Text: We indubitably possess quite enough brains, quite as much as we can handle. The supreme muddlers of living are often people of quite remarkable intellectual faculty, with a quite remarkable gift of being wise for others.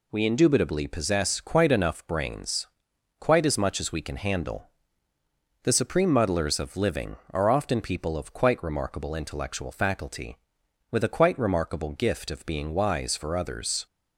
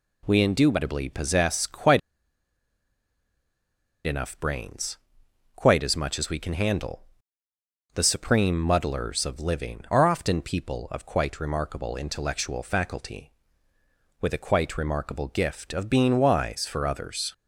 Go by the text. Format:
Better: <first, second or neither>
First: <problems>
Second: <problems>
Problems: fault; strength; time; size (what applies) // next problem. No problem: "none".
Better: first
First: none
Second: pauses between "quite" and "enough"; strong; at 1.9 s; 2.0 s long